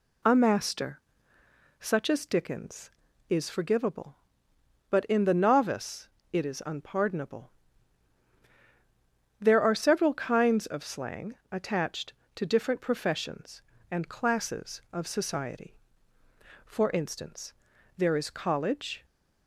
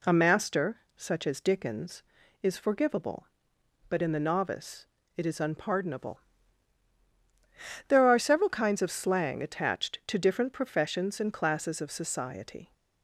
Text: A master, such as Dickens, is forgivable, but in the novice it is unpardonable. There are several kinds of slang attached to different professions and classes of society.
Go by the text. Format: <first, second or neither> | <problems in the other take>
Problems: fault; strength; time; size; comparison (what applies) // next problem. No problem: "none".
second | pauses between "novice" and "it"; slight; at 6.0 s; 0.24 s long; slight in the second // pauses between "slang" and "attached"; slight; at 11.3 s; 0.16 s long // goes on to say "For instance there is college"; strong; from 16.6 s on; 2.4 s long